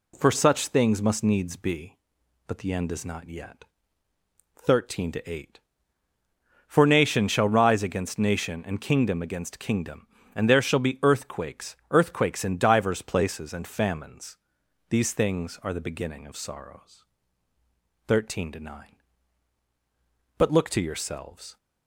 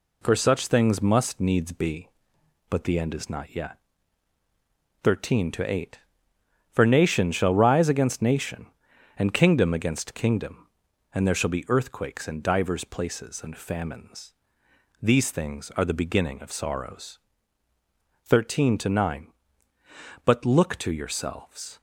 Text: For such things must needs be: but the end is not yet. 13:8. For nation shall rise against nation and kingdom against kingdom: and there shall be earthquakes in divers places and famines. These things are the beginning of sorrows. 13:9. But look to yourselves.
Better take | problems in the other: second | says "earthquakes" twice; at 11.9 s

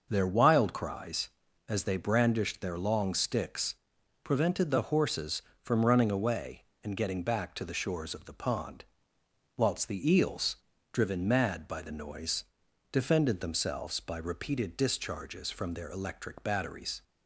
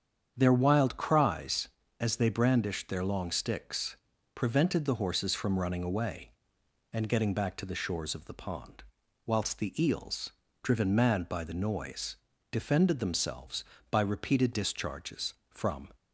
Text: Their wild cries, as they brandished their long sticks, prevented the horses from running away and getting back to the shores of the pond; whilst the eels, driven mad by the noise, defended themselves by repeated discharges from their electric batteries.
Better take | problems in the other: first | starts louder than the rest; strong; until 1.3 s; 8 dB; also in the first // stops before "their electric batteries"; at 15.9 s

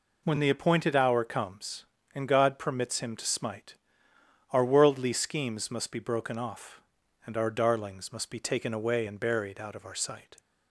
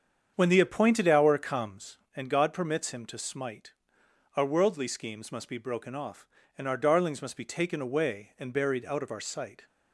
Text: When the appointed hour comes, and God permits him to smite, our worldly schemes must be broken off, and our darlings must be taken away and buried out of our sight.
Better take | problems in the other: first | starts louder than the rest; strong; until 1.8 s; 7.5 dB

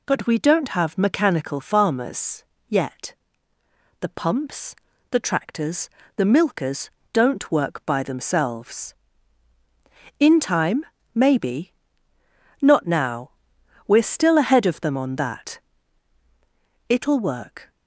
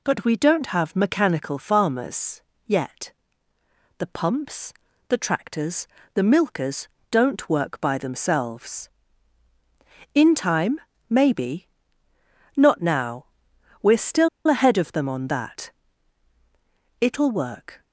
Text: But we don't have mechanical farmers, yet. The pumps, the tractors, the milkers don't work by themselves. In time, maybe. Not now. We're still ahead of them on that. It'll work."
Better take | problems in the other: first | pauses between "milkers" and "don't"; slight; at 6.8 s; 0.24 s long; slight in the first // pauses between "still" and "ahead"; slight; at 14.2 s; 0.19 s long

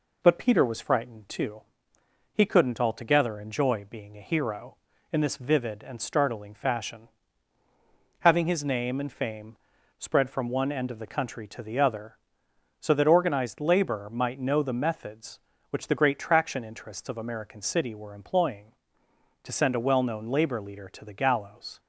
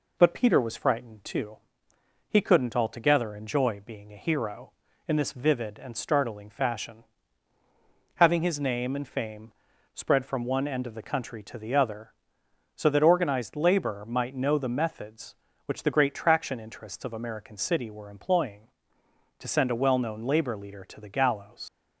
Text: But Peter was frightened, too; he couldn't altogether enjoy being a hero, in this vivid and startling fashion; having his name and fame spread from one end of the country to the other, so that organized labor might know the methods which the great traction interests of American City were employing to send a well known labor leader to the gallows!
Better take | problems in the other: first | pauses between "fame" and "spread"; at 9.5 s; 0.40 s long; also in the first // leaves "gallows" unfinished; at 21.6 s; 65 ms

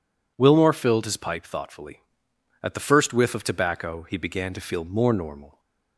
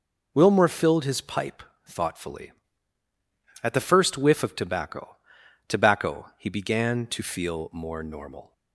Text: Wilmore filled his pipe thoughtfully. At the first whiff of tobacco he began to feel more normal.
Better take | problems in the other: first | pauses between "pipe" and "thoughtfully"; slight; at 1.6 s; 0.22 s long // says "tobacco" twice; at 5.6 s

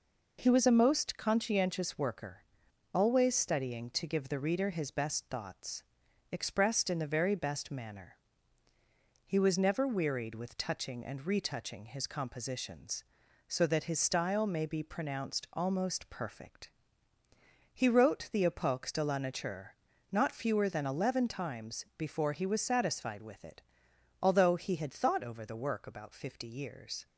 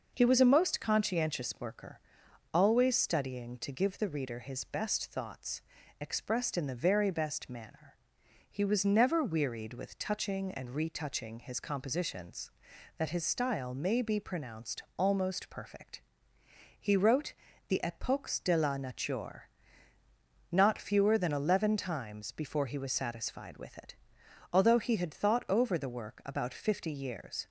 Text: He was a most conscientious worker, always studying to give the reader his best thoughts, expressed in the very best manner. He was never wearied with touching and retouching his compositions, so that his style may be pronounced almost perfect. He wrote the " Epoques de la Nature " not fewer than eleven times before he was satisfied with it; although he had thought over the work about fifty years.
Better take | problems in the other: first | skips "so"; at 12.7 s // pauses between "wrote" and "the"; slight; at 17.3 s; 0.34 s long

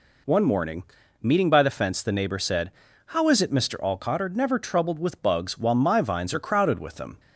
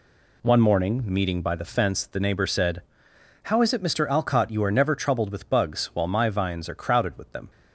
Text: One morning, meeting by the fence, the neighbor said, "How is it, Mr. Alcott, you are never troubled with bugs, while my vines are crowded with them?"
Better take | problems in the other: second | skips "you"; at 4.1 s

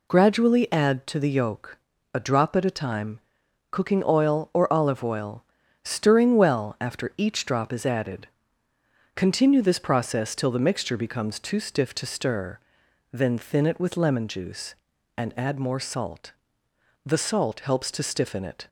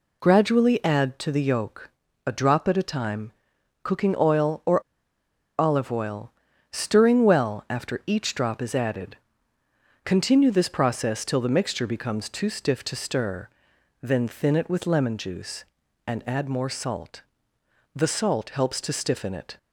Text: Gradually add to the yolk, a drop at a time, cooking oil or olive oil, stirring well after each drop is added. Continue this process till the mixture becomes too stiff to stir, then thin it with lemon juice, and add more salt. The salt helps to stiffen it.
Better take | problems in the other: first | pauses between "or" and "olive"; noticeable; at 4.8 s; 0.77 s long

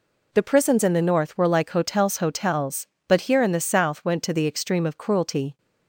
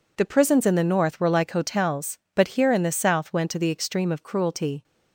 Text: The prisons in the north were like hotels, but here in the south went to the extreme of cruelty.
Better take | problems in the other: second | says "hotels" twice; at 2.1 s

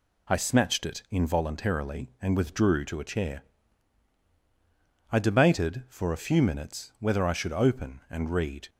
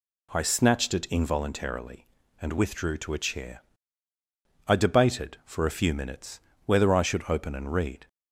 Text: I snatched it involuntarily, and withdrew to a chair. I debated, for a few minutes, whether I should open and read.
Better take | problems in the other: neither | none

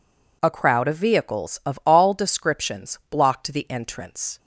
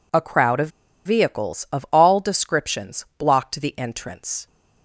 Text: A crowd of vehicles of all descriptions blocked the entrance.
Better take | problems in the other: first | pauses between "of" and "vehicles"; slight; at 0.6 s; 0.35 s long

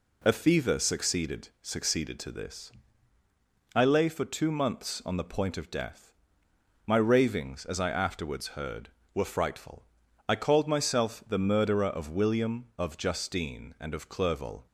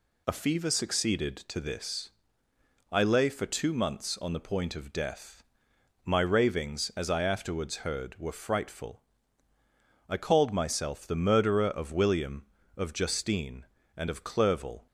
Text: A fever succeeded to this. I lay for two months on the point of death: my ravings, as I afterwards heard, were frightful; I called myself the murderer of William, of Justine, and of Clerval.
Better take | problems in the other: second | says "succeeded" twice; at 1.6 s

